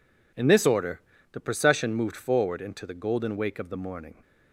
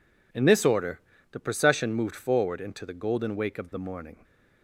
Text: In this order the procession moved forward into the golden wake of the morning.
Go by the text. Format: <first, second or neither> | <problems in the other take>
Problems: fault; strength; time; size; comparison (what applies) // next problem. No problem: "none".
neither | pauses between "order" and "the"; slight; the same in both